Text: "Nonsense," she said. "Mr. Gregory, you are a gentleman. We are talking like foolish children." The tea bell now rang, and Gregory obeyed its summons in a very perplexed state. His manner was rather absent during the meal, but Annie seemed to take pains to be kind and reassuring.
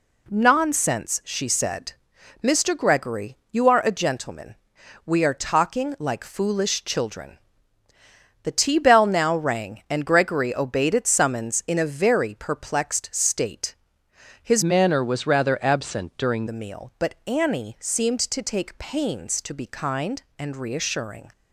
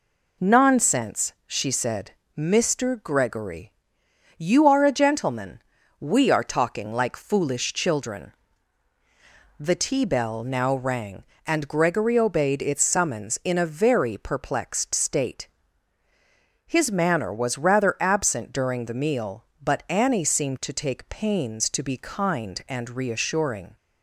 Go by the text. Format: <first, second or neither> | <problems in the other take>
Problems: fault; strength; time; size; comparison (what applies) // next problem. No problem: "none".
second | changes voice from "manner" to "during"; from 14.6 to 16.4 s; 1.8 s long